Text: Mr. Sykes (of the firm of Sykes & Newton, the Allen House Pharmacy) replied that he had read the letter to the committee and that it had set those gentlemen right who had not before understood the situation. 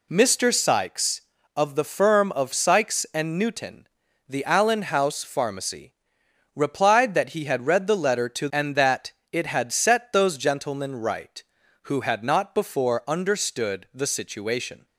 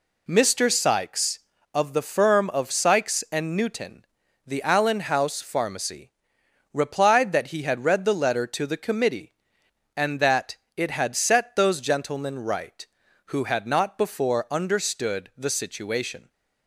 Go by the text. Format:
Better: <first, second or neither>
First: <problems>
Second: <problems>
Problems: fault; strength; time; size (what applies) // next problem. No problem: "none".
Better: second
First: skips "the committee"; at 8.5 s // pauses between "that" and "it"; slight; at 9.1 s; 0.20 s long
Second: pauses between "that" and "it"; slight; at 10.5 s; 0.20 s long